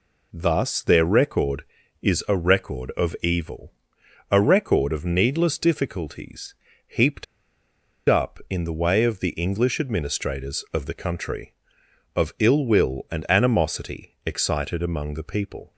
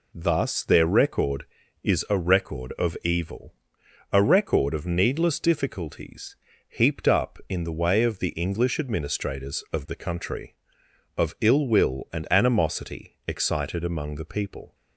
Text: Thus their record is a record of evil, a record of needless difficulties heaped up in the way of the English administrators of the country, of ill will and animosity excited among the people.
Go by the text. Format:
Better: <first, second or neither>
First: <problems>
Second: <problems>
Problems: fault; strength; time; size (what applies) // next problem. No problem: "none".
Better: second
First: pauses between "difficulties" and "heaped"; slight; at 6.5 s; 0.32 s long // pauses between "heaped" and "up"; noticeable; at 7.2 s; 0.83 s long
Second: pauses between "difficulties" and "heaped"; slight; at 6.3 s; 0.32 s long